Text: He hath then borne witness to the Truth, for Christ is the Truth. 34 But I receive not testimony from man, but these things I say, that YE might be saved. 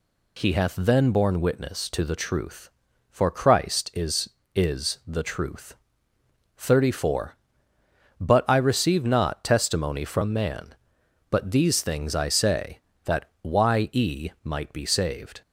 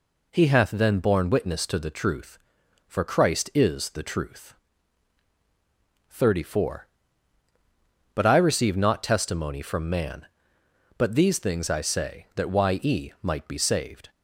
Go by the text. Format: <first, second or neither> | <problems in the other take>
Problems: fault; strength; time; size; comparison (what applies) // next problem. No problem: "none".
second | says "is" twice; at 4.5 s